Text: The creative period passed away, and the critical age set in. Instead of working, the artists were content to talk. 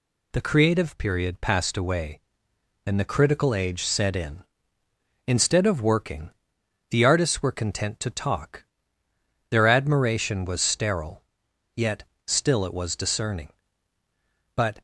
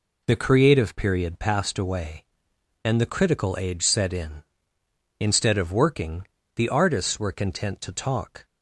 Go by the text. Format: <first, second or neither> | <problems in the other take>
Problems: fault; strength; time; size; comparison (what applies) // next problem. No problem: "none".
second | goes on to say "Their admiration was sterile yet still it was discerning But"; strong; from 9.5 s on; 5.3 s long